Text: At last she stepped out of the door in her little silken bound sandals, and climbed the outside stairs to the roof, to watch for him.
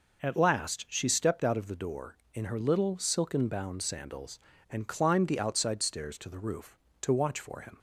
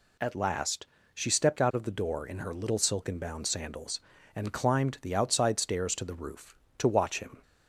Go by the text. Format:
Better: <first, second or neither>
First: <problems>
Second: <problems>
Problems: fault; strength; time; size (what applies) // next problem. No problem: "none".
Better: first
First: none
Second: pauses between "last" and "she"; slight; at 0.8 s; 0.30 s long // skips "for"; at 7.1 s